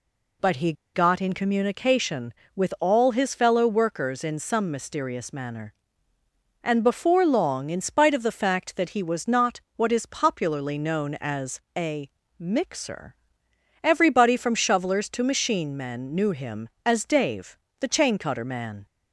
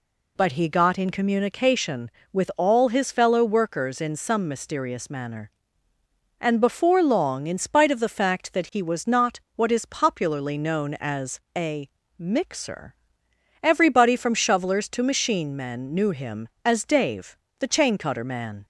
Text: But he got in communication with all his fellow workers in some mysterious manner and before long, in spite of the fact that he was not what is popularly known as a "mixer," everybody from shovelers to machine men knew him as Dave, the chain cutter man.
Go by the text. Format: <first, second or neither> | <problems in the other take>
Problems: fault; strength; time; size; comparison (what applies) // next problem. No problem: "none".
second | pauses between "he" and "got"; slight; at 0.7 s; 0.21 s long // pauses between "not" and "what"; slight; at 9.6 s; 0.16 s long; slight in the second // pauses between "as" and "a"; slight; at 11.6 s; 0.16 s long; slight in the second // pauses between "a" and "mixer"; slight; at 12.0 s; 0.28 s long; slight in the second